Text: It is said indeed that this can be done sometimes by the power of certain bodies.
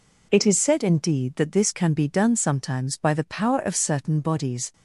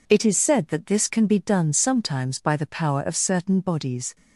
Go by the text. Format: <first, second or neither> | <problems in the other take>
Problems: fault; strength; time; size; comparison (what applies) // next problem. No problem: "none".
first | skips "indeed"; at 0.6 s